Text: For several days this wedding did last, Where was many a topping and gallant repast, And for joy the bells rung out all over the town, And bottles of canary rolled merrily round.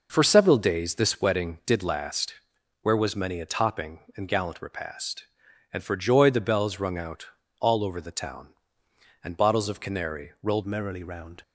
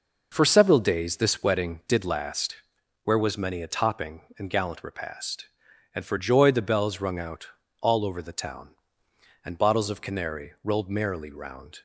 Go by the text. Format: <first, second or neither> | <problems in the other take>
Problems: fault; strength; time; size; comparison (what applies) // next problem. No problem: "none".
second | pauses between "out" and "all"; slight; at 7.2 s; 0.34 s long; slight in the second // changes voice at "merrily"; from 10.6 s on; 0.8 s long